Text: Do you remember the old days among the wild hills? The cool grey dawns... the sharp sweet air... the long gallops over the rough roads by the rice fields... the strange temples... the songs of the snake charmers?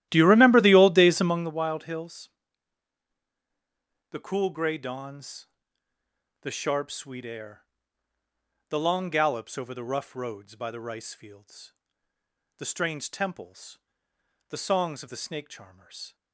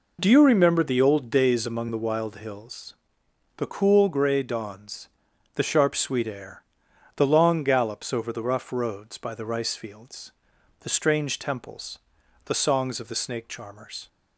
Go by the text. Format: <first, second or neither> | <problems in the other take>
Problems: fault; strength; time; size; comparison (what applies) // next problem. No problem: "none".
second | starts louder than the rest; strong; until 1.6 s; 14 dB